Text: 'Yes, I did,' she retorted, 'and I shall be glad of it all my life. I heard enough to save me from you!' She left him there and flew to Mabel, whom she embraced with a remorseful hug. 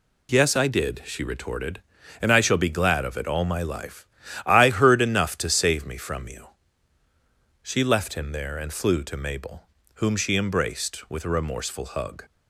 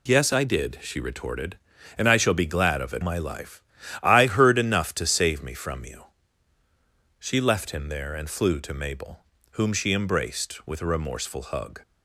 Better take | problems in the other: first | skips "all"; at 3.0 s

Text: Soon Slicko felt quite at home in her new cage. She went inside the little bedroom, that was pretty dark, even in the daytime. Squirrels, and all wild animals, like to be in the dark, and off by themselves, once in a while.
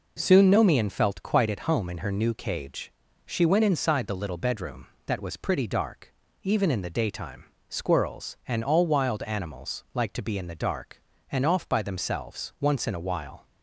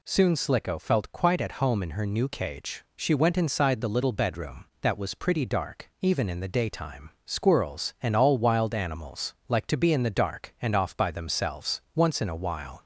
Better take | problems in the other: second | says "Nomian" for "Slicko"; at 0.4 s

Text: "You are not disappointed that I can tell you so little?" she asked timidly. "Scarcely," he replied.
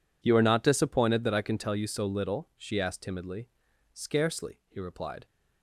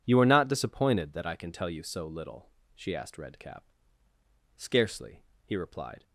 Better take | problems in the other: first | says "redcap" for "timidly"; at 3.1 s

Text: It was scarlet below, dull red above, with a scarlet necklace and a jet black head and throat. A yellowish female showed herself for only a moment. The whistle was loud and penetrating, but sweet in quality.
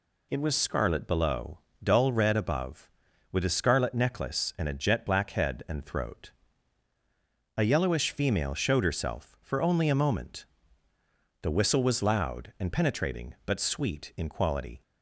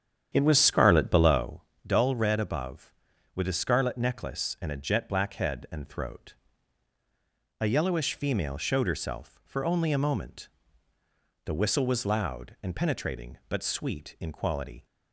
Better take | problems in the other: first | starts louder than the rest; strong; until 1.6 s; 9 dB

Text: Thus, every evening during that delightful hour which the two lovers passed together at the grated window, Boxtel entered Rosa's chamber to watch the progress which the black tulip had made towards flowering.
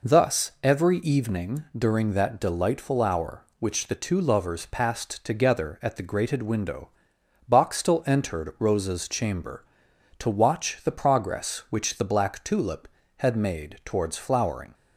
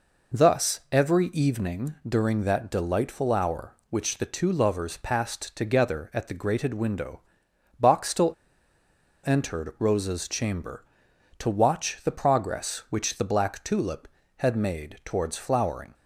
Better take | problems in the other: first | pauses between "evening" and "during"; slight; at 1.9 s; 0.16 s long; slight in the first // pauses between "Boxtel" and "entered"; noticeable; at 8.3 s; 0.94 s long

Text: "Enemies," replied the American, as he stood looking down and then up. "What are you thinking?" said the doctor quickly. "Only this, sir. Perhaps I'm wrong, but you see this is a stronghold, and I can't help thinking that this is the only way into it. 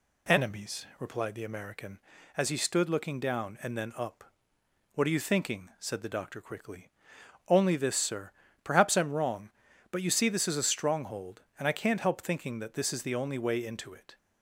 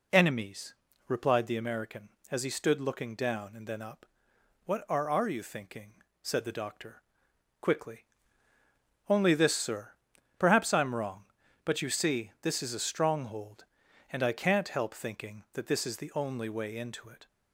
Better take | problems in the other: first | says "are" twice; at 5.0 s // pauses between "doctor" and "quickly"; noticeable; at 7.0 s; 0.58 s long

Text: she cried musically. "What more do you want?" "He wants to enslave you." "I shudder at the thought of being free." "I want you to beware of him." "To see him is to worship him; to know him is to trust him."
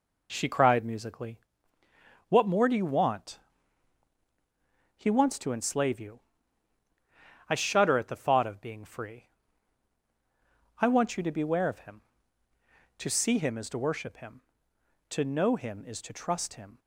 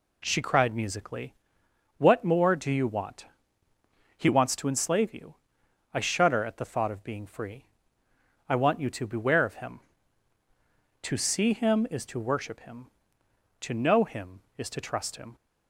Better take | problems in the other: neither | none

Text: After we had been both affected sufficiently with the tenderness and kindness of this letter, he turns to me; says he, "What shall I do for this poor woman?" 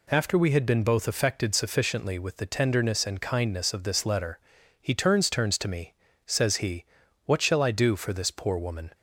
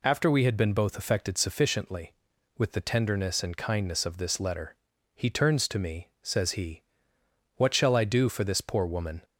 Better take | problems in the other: second | says "turns" twice; at 5.2 s

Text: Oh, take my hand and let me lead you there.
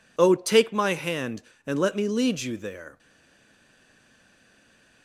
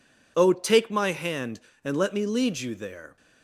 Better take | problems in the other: second | stays silent after the last word; noticeable; from 2.9 s on; 2.1 s long

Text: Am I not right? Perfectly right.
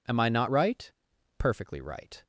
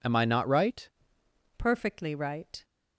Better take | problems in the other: first | changes voice at "Perfectly"; from 1.5 s on; 1.1 s long

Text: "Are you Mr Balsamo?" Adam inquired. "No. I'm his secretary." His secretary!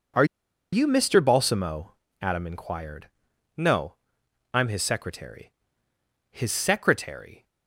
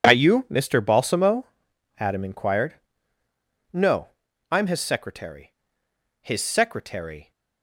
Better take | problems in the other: second | pauses between "Are" and "you"; noticeable; at 0.2 s; 0.47 s long

